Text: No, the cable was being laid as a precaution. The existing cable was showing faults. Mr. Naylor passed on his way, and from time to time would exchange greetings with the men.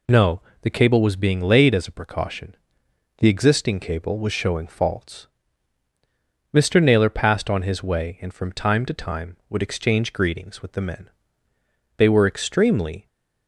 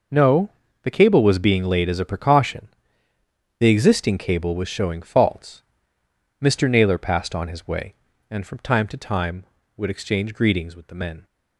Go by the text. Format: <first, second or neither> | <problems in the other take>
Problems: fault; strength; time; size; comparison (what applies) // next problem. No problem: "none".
second | goes on to say "They were extremely"; noticeable; from 11.9 s on; 1.1 s long